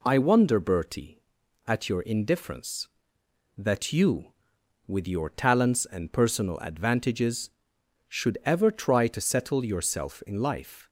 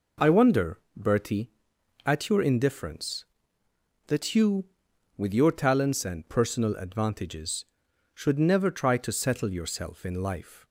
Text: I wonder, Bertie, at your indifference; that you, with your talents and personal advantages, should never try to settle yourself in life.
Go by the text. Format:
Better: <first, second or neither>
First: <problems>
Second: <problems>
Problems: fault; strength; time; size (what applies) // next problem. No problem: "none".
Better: second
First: says "ever" for "never"; at 8.4 s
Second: none